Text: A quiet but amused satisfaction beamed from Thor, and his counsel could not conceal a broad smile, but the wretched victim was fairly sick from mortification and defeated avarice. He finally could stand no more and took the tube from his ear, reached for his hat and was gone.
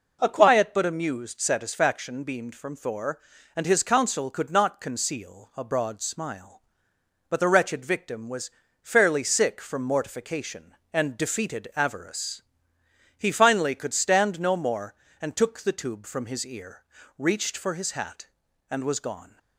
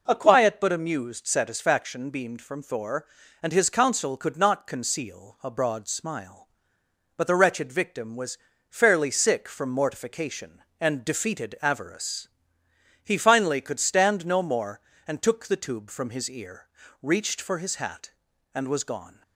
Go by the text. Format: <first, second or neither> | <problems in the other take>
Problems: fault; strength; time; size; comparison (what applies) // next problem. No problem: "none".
neither | pauses between "was" and "fairly"; slight; the same in both